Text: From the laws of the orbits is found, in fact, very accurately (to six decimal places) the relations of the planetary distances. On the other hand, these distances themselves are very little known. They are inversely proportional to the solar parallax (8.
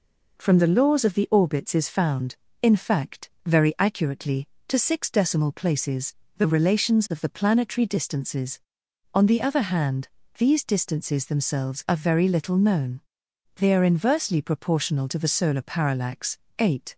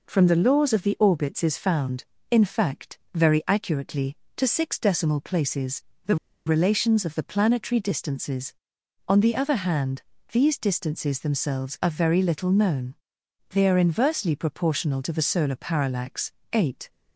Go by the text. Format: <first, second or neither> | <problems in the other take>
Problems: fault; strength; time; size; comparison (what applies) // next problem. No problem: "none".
first | pauses between "the" and "relations"; slight; at 6.1 s; 0.30 s long